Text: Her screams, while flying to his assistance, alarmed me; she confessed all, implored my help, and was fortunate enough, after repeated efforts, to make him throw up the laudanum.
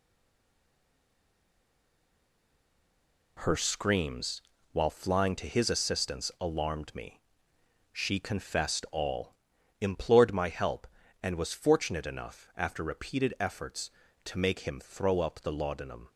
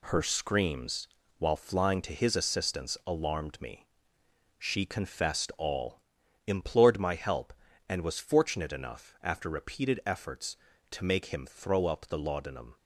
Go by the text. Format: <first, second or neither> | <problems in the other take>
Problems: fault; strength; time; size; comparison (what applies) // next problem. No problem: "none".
second | stays silent before the first word; strong; until 3.3 s; 3.3 s long